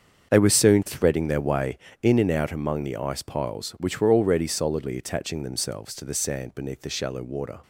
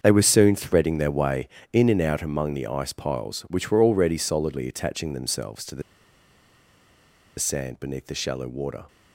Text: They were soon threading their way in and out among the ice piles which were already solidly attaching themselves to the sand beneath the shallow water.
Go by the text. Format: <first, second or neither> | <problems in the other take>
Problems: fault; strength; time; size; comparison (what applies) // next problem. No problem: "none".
first | starts louder than the rest; until 1.0 s; 7 dB; also in the first // pauses between "the" and "sand"; strong; at 5.8 s; 1.5 s long